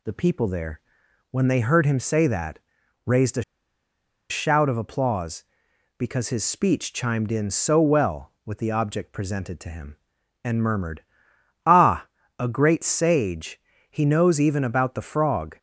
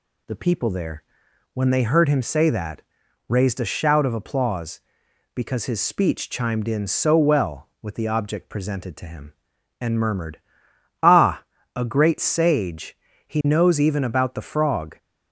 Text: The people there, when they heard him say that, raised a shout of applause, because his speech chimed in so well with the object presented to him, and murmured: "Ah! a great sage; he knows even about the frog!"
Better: second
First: pauses between "a" and "shout"; noticeable; at 3.4 s; 0.88 s long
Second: none

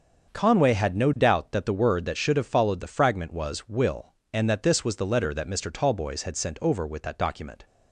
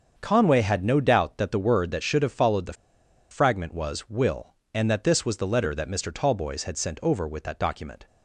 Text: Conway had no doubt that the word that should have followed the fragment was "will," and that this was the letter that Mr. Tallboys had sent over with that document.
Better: first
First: starts louder than the rest; until 1.3 s; 7 dB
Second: starts louder than the rest; until 1.1 s; 7 dB // pauses between "the" and "fragment"; noticeable; at 2.7 s; 0.58 s long

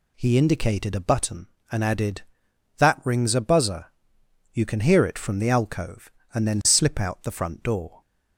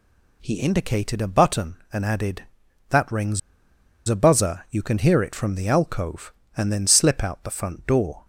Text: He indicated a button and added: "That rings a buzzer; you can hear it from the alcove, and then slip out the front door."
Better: first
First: none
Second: pauses between "rings" and "a"; noticeable; at 3.3 s; 0.69 s long

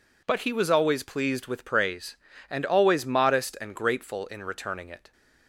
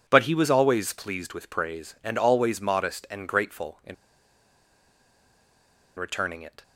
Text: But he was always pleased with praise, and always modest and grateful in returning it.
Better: first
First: none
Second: pauses between "in" and "returning"; strong; at 3.9 s; 2.0 s long

